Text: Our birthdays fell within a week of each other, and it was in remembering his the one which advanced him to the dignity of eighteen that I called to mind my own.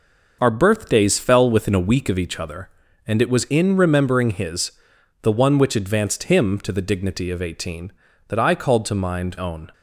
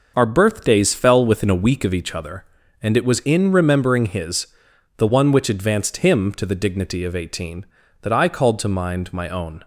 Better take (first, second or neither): second